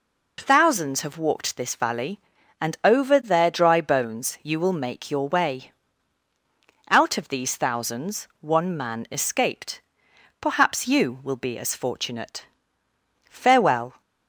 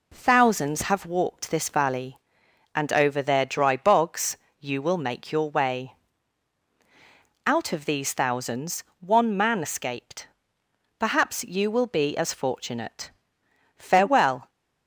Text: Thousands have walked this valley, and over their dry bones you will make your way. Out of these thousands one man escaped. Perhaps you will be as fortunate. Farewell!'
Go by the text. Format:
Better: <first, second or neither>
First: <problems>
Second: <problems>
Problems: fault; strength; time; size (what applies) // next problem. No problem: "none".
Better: first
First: none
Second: says "bogs" for "bones"; at 3.7 s // pauses between "thousands" and "one"; slight; at 8.8 s; 0.16 s long